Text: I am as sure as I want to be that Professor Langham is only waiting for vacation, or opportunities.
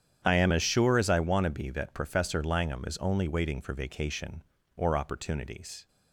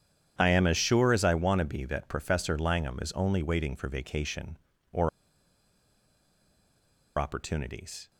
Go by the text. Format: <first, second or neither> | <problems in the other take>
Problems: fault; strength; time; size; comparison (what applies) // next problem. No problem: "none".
first | starts louder than the rest; strong; until 1.3 s; 9.5 dB; strong in the first // pauses between "or" and "opportunities"; strong; at 5.0 s; 2.0 s long